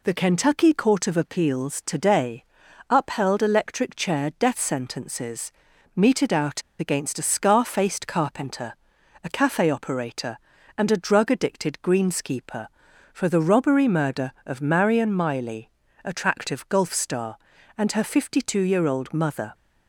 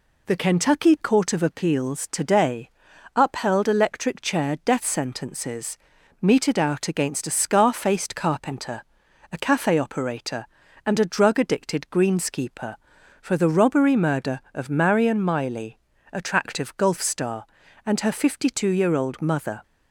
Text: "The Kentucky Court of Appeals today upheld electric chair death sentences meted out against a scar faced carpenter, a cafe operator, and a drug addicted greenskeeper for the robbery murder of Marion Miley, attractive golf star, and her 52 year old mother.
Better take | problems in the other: second | pauses between "today" and "upheld"; noticeable; at 2.4 s; 0.48 s long; noticeable in the second // pauses between "sentences" and "meted"; at 5.5 s; 0.42 s long; also in the second // pauses between "out" and "against"; slight; at 6.6 s; 0.18 s long

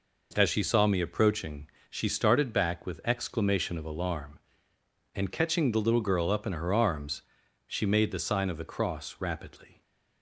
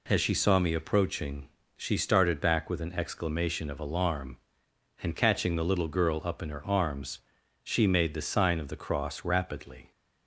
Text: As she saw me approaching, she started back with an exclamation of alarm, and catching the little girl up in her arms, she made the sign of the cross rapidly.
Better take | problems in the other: second | skips "an"; at 3.0 s

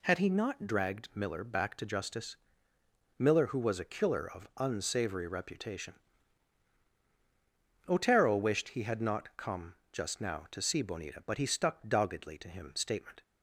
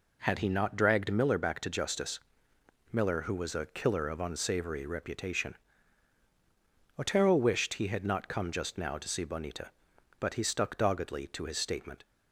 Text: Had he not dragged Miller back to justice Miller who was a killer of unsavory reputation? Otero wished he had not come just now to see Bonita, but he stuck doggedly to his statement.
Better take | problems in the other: second | pauses between "justice" and "Miller"; noticeable; at 2.3 s; 0.82 s long; noticeable in the second // pauses between "come" and "just"; slight; at 9.7 s; 0.18 s long // says "him" for "his"; at 12.4 s

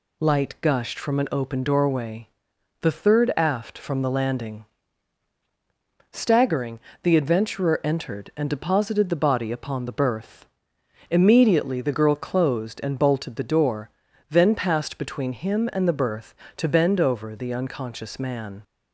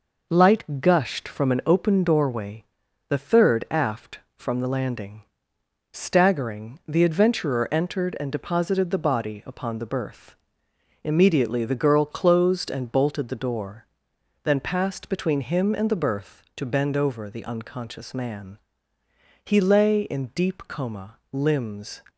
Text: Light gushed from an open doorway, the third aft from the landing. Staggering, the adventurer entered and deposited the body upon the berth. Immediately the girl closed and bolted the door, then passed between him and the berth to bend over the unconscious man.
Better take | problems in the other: first | goes on to say "He lay in deep coma limbs"; strong; from 19.4 s on; 2.5 s long

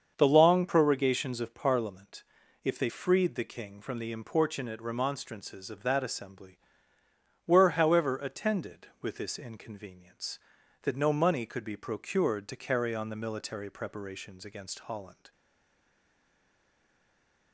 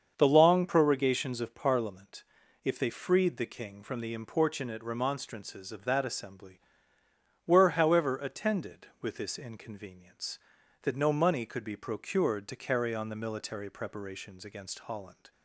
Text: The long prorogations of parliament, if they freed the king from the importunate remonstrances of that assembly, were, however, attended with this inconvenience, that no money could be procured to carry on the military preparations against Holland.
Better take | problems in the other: second | starts louder than the rest; until 1.1 s; 7 dB; also in the second // stays silent after the last word; from 15.3 s on; 2.2 s long

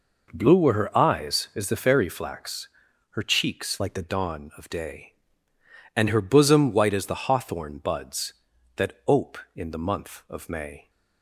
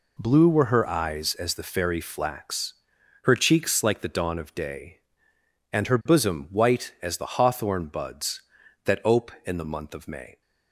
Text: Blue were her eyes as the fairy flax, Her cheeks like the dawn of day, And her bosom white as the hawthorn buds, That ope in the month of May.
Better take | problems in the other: second | changes voice from "like" to "the"; from 3.7 to 4.0 s; 0.3 s long

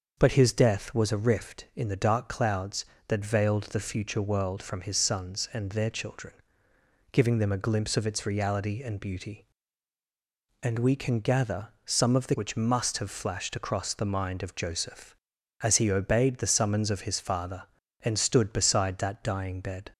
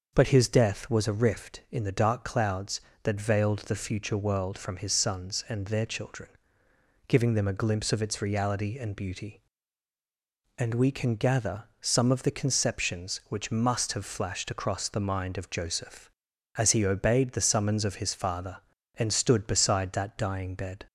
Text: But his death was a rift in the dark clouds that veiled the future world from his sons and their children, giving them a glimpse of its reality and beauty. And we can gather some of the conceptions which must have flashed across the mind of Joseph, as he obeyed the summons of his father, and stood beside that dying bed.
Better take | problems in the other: second | starts louder than the rest; noticeable; until 1.1 s; 6 dB; noticeable in the second // pauses between "gather" and "some"; slight; at 11.6 s; 0.16 s long; slight in the second // skips "conceptions"; at 12.3 s

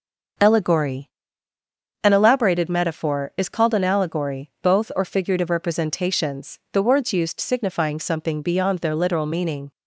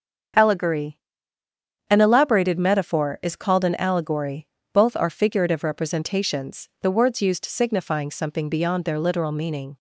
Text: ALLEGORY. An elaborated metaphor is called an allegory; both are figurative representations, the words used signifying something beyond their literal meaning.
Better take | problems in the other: second | starts louder than the rest; until 2.3 s; 6.5 dB; strong in the second // says "or" for "are"; at 4.9 s

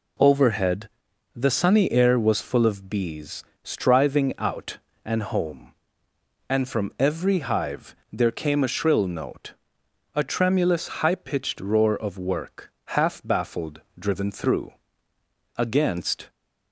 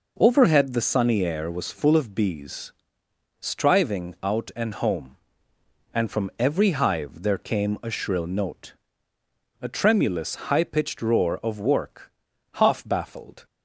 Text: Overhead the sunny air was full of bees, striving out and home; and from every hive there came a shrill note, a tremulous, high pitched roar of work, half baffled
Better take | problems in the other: second | pauses between "Overhead" and "the"; noticeable; at 0.8 s; 0.48 s long // pauses between "hive" and "there"; slight; at 7.9 s; 0.18 s long // goes on to say "driven through against"; strong; from 13.9 s on; 2.3 s long

